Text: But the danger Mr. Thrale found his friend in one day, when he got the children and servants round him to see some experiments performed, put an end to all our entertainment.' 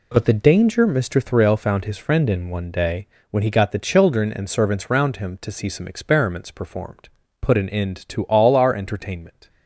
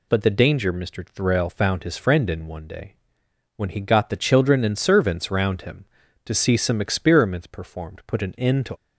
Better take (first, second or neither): first